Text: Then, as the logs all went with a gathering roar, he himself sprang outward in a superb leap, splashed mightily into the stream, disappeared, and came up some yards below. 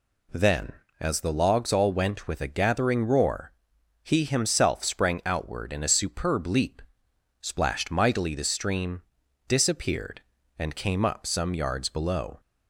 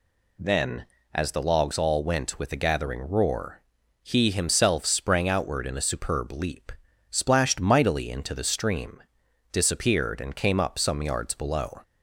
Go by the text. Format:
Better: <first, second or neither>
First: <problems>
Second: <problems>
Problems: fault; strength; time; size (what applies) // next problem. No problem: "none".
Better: second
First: skips "into"; at 8.3 s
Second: none